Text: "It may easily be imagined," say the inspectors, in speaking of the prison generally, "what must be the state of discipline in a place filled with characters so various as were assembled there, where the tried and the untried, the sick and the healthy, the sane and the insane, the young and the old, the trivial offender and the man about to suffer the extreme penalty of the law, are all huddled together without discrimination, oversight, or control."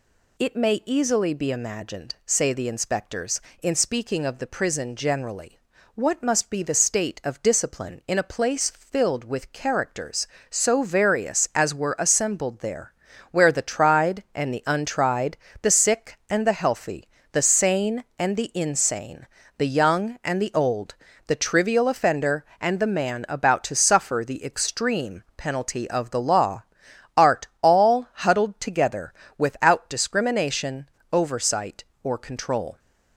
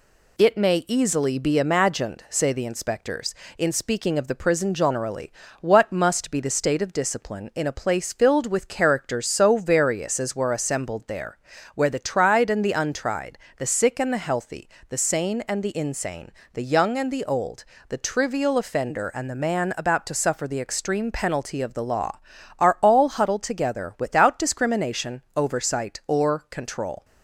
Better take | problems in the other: second | says "art" for "are"; at 27.1 s // pauses between "together" and "without"; slight; at 29.1 s; 0.28 s long

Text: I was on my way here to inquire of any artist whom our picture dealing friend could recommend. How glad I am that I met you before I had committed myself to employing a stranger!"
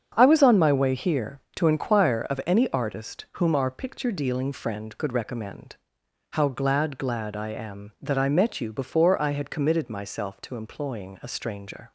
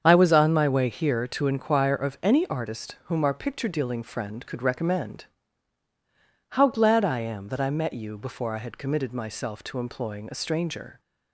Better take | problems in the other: second | starts louder than the rest; strong; until 1.1 s; 7.5 dB; strong in the second // says "glad" twice; at 6.9 s

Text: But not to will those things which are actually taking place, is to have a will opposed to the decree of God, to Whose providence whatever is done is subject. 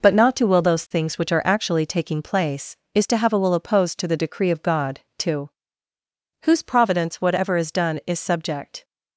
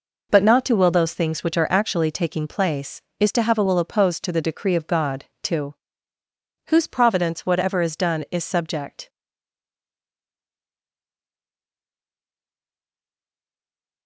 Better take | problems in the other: first | pauses between "to" and "Whose"; noticeable; at 5.7 s; 0.94 s long; noticeable in the first // stays silent after the last word; strong; from 9.0 s on; 5.0 s long

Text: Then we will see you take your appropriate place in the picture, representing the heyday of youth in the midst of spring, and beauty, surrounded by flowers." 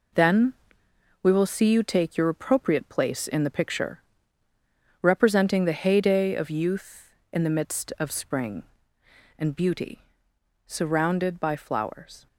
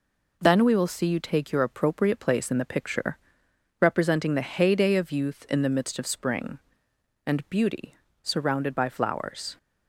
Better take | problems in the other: second | gets quieter; strong; throughout; 7.5 dB // pauses between "Then" and "we"; noticeable; at 0.5 s; 0.70 s long

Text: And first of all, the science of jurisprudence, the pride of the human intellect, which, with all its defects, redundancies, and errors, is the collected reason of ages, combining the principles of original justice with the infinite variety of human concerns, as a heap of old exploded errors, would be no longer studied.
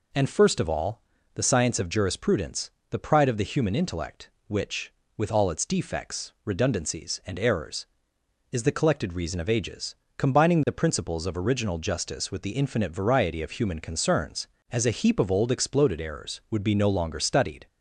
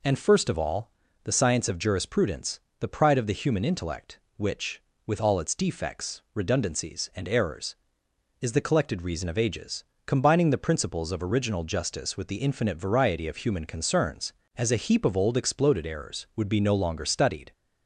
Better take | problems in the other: neither | none

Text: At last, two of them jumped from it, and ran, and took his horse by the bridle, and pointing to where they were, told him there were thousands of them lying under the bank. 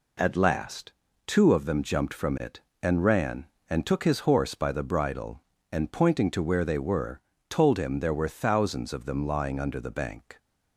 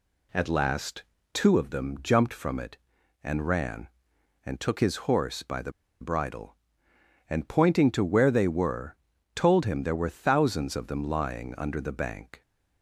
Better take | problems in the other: first | pauses between "the" and "bridle"; slight; at 5.7 s; 0.29 s long

